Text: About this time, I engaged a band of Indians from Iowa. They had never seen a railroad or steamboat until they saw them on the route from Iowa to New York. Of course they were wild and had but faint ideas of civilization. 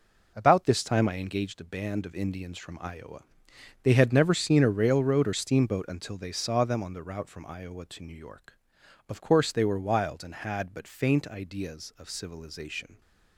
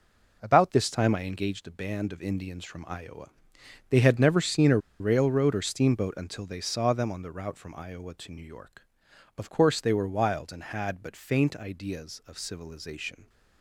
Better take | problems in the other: first | pauses between "a" and "railroad"; slight; at 4.7 s; 0.22 s long

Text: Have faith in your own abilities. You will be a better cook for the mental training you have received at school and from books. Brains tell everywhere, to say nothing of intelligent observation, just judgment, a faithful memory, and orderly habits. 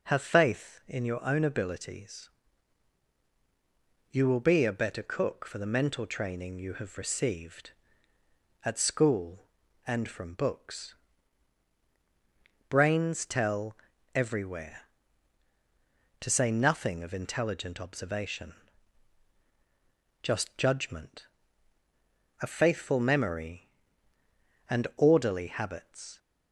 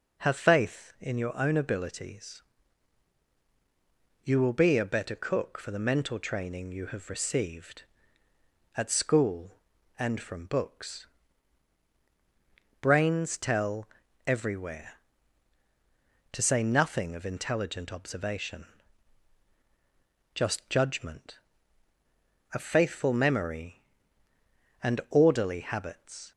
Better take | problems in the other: neither | pauses between "tell" and "everywhere"; the same in both

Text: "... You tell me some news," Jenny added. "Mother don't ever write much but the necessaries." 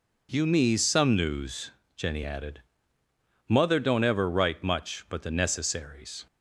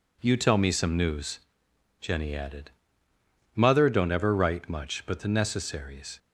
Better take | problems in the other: second | skips "tell"; at 0.4 s

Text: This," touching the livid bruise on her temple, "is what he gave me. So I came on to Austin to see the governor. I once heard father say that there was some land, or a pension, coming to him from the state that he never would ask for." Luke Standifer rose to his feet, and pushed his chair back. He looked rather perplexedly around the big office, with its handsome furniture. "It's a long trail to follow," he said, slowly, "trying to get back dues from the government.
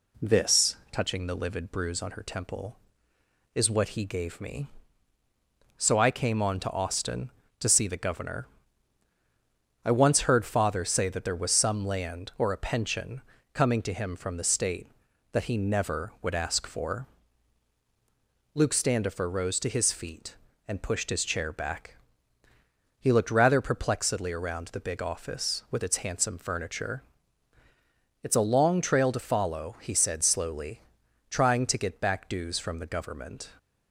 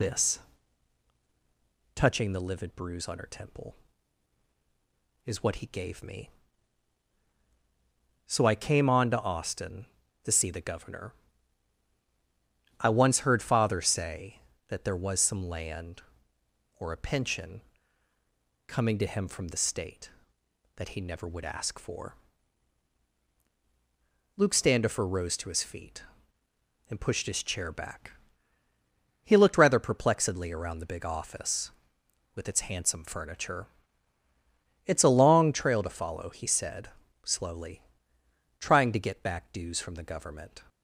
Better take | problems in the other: first | loses the start of "This"; at 0.0 s; 40 ms

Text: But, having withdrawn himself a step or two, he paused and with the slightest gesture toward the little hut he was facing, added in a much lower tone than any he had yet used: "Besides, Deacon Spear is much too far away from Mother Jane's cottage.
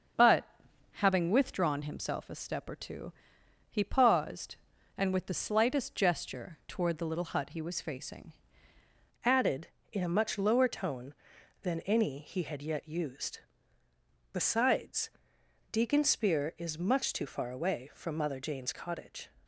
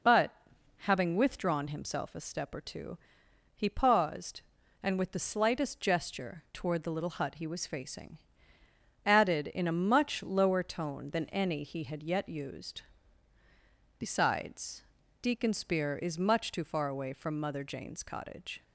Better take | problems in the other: second | starts louder than the rest; until 1.6 s; 6.5 dB // changes voice at "added"; from 9.2 s on; 10.0 s long

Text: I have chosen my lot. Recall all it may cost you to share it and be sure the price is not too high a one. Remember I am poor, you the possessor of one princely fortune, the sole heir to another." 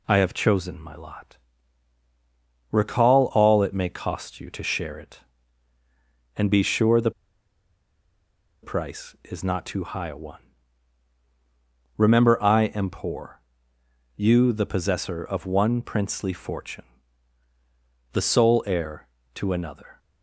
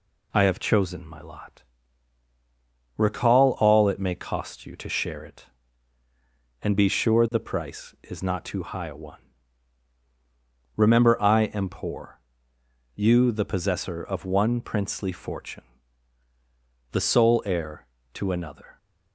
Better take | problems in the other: second | pauses between "the" and "price"; strong; at 7.1 s; 1.5 s long

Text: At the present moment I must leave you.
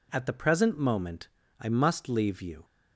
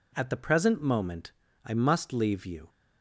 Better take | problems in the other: neither | pauses between "moment" and "I"; slight; the same in both

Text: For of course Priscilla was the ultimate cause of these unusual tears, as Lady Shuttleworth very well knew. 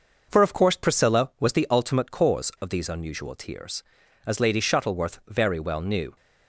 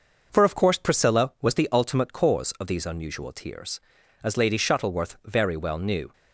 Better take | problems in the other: neither | none

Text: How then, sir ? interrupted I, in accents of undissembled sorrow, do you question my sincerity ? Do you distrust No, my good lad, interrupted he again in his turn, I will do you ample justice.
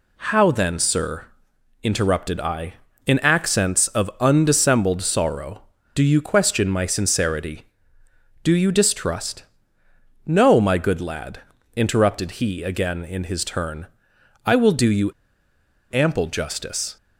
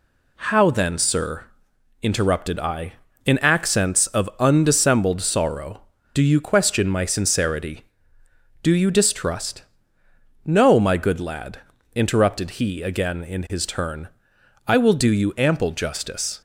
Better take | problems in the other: second | pauses between "distrust" and "No"; noticeable; at 9.4 s; 0.82 s long; noticeable in the second // pauses between "you" and "ample"; noticeable; at 15.1 s; 0.81 s long

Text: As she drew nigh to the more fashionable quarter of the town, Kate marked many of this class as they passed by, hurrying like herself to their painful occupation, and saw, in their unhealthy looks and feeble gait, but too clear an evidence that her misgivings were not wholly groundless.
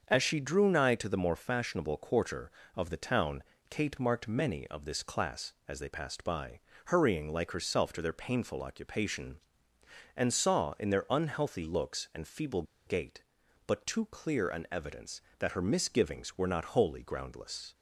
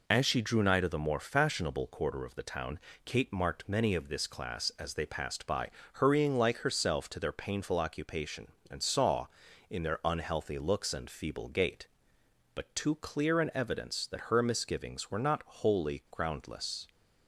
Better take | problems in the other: second | starts louder than the rest; until 1.1 s; 6.5 dB // pauses between "feeble" and "gait"; slight; at 12.6 s; 0.23 s long

